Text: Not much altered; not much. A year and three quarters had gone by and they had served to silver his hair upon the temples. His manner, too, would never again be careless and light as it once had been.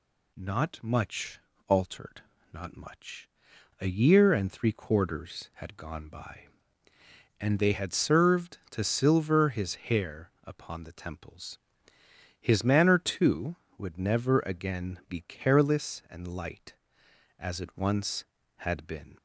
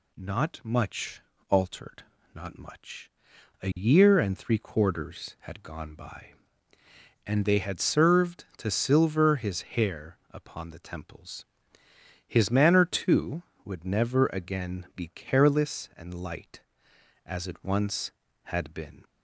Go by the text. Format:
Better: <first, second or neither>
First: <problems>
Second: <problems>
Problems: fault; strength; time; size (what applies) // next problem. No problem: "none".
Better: neither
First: pauses between "much" and "altered"; slight; at 1.3 s; 0.28 s long // pauses between "hair" and "upon"; slight; at 10.2 s; 0.16 s long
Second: pauses between "much" and "altered"; slight; at 1.2 s; 0.28 s long // pauses between "hair" and "upon"; slight; at 10.1 s; 0.16 s long